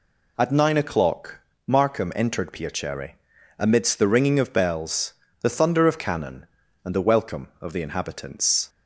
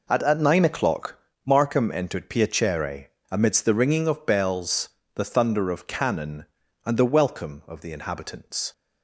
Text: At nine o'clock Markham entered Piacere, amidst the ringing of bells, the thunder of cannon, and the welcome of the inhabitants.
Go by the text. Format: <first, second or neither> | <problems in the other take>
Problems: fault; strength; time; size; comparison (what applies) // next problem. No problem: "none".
first | says "At" twice; at 0.2 s // pauses between "o'clock" and "Markham"; slight; at 1.1 s; 0.28 s long; slight in the first